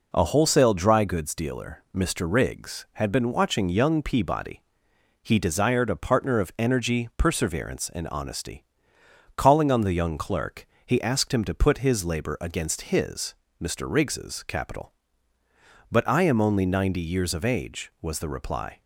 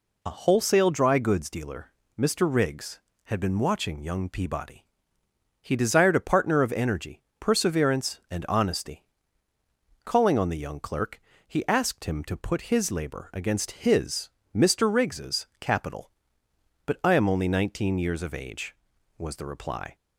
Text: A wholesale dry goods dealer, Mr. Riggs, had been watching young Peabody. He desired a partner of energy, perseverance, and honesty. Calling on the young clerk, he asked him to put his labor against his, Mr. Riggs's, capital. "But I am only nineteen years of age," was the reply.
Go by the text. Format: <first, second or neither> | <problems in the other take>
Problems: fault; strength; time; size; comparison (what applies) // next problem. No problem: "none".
second | says "ninety" for "nineteen"; at 16.6 s